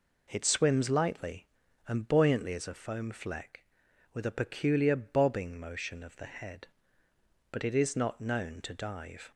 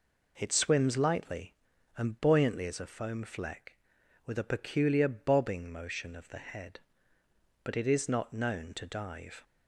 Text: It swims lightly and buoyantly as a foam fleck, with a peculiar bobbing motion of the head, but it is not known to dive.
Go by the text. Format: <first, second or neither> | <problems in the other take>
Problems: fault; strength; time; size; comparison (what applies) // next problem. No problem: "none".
neither | none